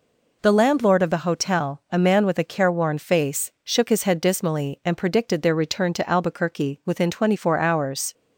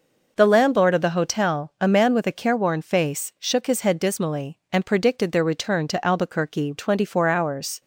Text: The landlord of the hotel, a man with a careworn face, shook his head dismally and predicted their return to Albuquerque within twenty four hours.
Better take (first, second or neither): first